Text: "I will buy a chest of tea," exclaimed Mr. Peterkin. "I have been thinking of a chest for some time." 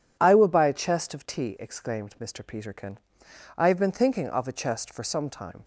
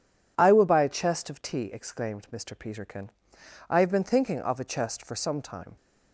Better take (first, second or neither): neither